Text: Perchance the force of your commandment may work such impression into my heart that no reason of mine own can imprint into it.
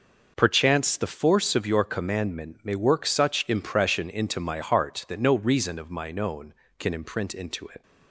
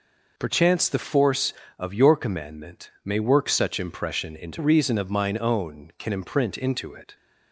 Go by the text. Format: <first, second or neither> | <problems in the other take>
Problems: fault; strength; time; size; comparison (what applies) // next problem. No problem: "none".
first | pauses between "commandment" and "may"; slight; at 2.8 s; 0.16 s long // skips "my heart that no"; at 4.5 s